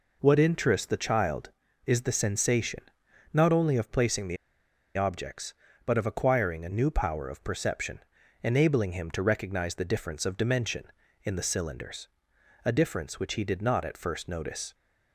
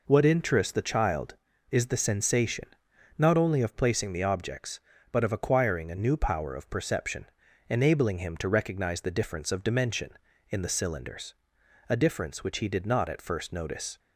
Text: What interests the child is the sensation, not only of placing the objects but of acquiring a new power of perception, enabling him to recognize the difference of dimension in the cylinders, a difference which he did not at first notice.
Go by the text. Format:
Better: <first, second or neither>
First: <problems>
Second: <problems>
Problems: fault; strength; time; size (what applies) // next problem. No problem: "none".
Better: second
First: pauses between "the" and "objects"; noticeable; at 4.3 s; 0.59 s long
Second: none